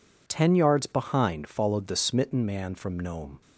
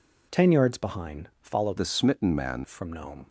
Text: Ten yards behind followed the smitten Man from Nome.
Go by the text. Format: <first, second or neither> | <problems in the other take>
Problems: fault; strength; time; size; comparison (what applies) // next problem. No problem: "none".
first | changes voice from "the" to "Man"; from 1.7 to 2.6 s; 0.9 s long